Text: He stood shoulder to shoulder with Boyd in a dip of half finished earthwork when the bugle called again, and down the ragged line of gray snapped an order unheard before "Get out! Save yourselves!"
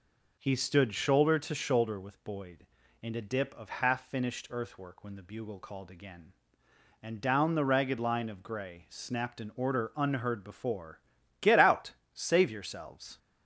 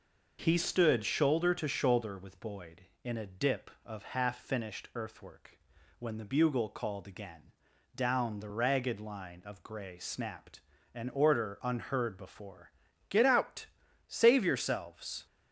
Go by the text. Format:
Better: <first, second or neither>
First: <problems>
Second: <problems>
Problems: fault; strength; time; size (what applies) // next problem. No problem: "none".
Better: first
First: pauses between "before" and "Get"; at 11.0 s; 0.40 s long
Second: pauses between "earthwork" and "when"; at 5.5 s; 0.40 s long // skips "and"; at 7.7 s // pauses between "snapped" and "an"; slight; at 10.6 s; 0.32 s long // pauses between "before" and "Get"; at 12.7 s; 0.38 s long